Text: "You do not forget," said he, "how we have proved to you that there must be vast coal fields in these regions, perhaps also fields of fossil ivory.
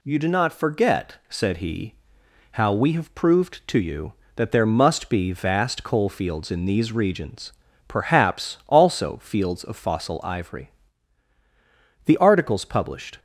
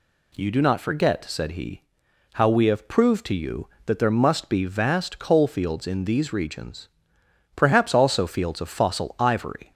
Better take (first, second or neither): second